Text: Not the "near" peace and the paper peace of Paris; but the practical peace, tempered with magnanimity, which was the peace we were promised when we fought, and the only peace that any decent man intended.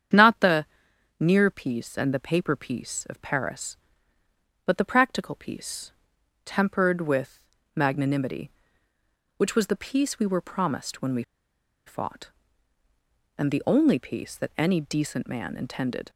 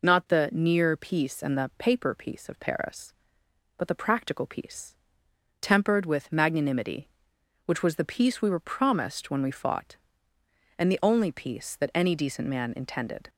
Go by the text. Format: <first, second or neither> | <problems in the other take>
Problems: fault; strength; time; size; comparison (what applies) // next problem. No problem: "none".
second | starts louder than the rest; strong; until 1.6 s; 8.5 dB // pauses between "the" and "near"; noticeable; at 0.6 s; 0.52 s long // pauses between "with" and "magnanimity"; slight; at 7.3 s; 0.34 s long // pauses between "we" and "fought"; noticeable; at 11.2 s; 0.64 s long